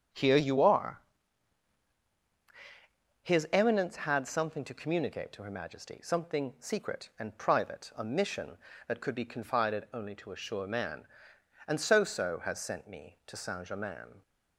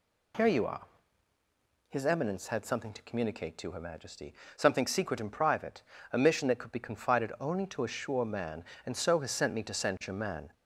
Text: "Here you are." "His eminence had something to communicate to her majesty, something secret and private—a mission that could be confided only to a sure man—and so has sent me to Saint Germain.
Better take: second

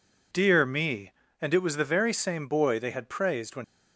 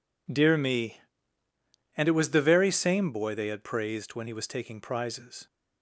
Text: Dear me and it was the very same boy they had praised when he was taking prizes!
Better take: second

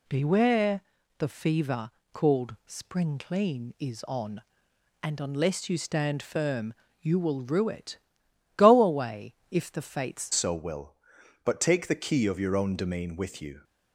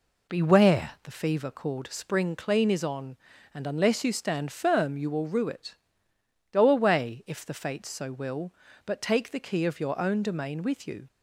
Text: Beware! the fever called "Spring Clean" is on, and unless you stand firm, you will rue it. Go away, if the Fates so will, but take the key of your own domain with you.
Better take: second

